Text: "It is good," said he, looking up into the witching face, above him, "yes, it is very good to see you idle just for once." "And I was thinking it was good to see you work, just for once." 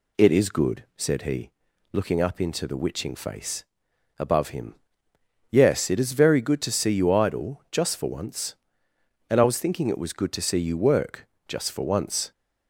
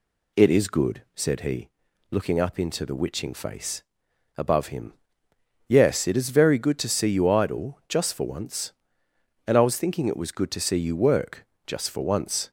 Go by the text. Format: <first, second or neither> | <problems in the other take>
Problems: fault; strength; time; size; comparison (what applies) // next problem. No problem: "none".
neither | none